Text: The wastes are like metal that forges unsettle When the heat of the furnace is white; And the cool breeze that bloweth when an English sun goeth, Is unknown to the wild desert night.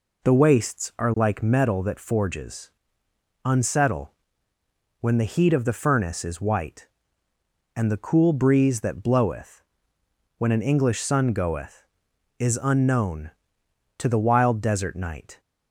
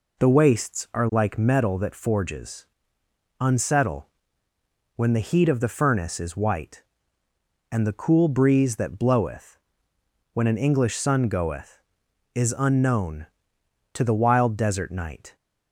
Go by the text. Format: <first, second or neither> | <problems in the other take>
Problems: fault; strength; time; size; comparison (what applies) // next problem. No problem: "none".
neither | pauses between "forges" and "unsettle"; noticeable; the same in both // pauses between "unsettle" and "When"; noticeable; the same in both // pauses between "bloweth" and "when"; noticeable; the same in both